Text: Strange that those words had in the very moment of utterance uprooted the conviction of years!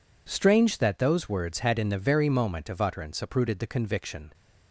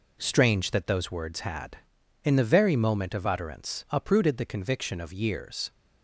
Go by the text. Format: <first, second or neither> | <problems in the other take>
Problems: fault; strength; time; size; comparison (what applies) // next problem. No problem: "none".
second | stops before "of years"; at 4.3 s